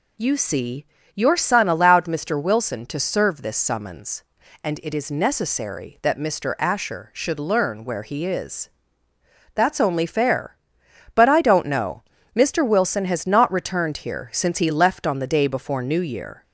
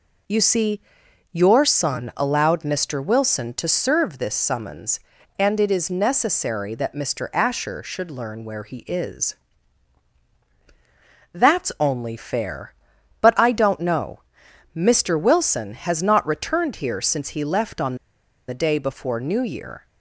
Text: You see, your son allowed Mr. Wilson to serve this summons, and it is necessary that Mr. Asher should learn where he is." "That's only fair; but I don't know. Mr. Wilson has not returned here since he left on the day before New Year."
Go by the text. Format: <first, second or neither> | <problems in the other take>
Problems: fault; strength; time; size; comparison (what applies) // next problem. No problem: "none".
first | pauses between "on" and "the"; noticeable; at 17.9 s; 0.53 s long